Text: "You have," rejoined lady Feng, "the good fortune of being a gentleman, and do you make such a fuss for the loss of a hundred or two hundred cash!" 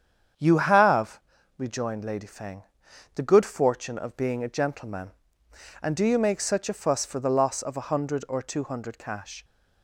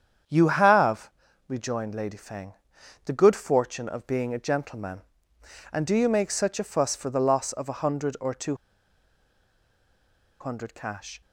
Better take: first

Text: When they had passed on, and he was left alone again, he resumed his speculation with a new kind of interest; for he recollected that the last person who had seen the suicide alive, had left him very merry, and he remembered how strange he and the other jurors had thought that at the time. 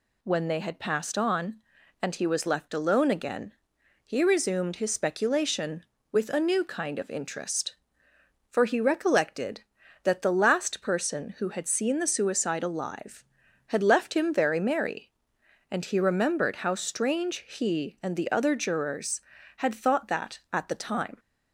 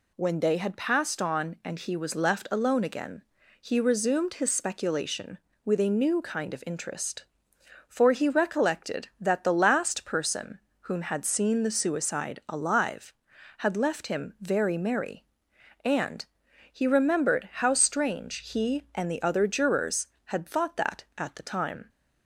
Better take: first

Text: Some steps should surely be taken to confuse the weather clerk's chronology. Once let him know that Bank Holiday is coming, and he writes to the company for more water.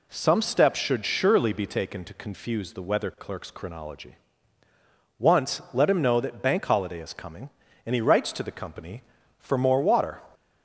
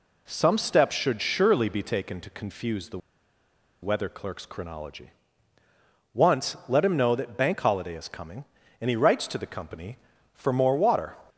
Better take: first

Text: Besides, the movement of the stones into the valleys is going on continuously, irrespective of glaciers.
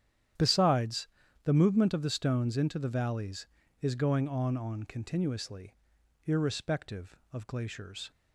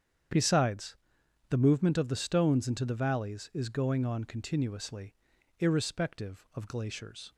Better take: second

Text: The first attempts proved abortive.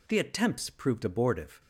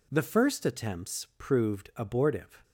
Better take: second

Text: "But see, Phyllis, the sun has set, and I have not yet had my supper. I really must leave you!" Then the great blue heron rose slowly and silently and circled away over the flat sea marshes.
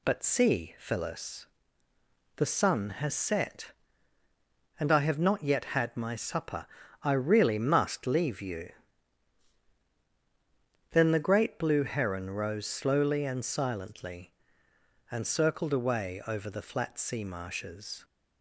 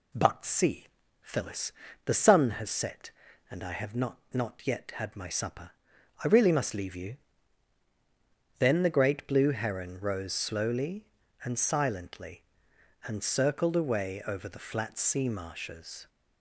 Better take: first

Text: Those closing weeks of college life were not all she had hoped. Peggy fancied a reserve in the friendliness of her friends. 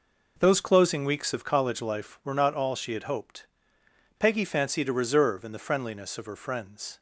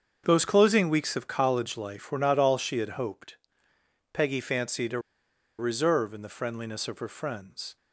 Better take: first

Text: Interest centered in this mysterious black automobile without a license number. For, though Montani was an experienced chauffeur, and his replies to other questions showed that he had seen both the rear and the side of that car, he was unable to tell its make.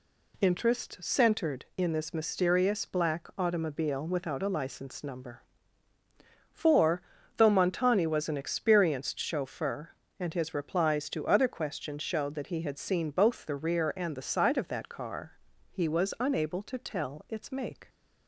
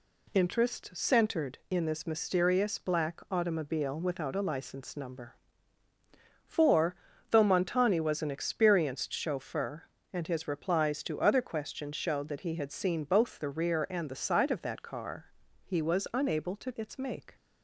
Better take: first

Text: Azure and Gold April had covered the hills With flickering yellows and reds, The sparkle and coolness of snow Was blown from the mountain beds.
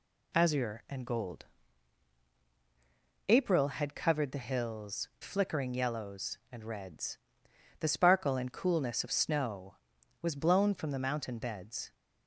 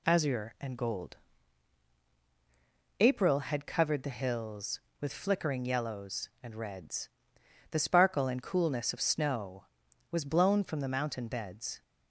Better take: second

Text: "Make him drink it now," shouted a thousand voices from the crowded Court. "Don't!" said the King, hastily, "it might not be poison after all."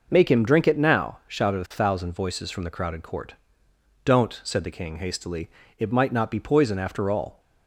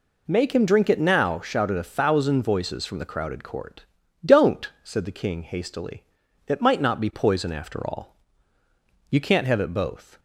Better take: first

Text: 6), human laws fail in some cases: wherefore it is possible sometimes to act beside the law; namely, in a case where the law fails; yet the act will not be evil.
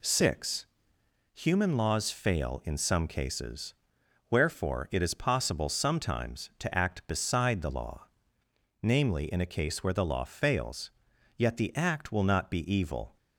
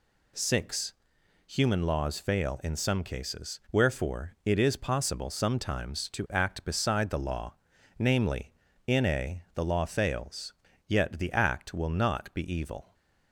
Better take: first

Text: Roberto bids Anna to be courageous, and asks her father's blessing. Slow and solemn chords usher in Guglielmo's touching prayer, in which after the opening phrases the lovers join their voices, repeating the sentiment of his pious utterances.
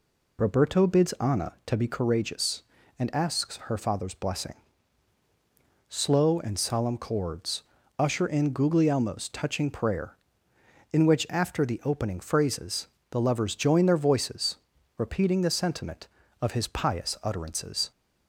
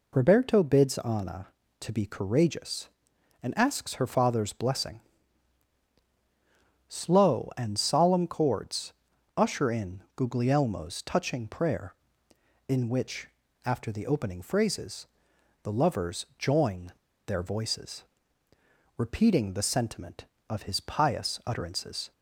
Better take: first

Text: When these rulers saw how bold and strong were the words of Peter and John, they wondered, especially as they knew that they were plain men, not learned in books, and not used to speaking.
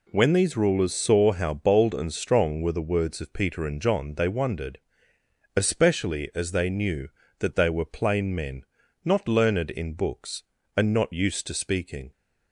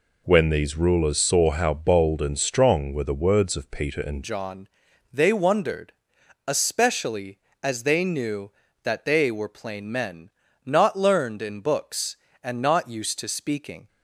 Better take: first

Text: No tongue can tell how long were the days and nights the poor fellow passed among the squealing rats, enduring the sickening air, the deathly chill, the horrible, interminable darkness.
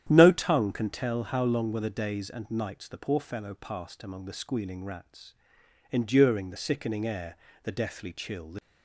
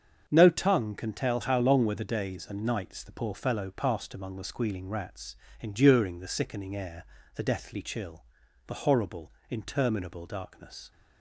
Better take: second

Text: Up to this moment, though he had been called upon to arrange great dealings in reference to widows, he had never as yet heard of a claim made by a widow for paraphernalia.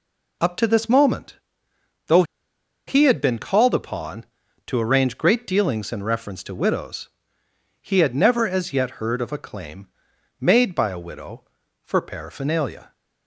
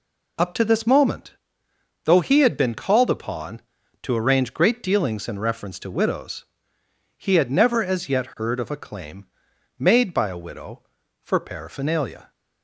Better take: second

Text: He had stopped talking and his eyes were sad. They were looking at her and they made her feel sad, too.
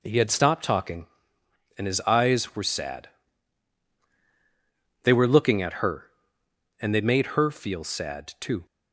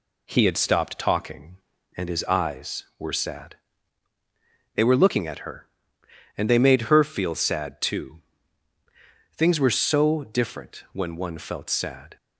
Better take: first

